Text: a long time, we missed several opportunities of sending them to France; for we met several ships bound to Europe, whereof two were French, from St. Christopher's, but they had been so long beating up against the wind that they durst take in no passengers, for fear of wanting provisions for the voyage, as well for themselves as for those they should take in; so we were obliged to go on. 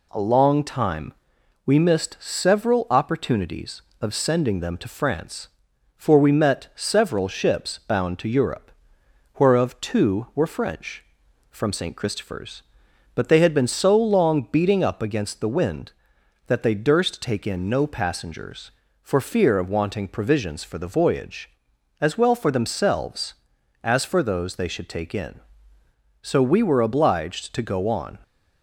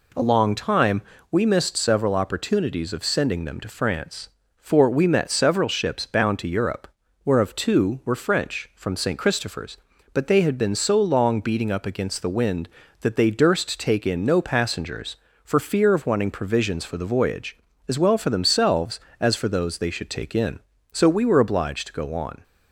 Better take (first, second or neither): neither